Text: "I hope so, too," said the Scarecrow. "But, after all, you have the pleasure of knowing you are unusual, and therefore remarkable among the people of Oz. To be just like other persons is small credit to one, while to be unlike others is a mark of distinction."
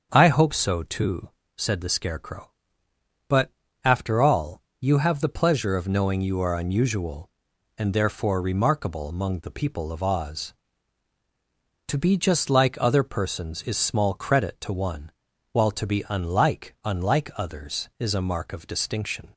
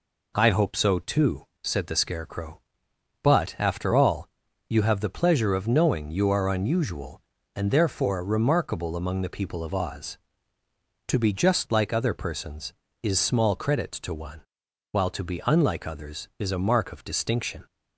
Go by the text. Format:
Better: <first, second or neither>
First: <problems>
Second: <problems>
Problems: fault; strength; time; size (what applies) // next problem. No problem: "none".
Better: second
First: starts louder than the rest; until 1.1 s; 7 dB // says "unlike" twice; at 16.8 s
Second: none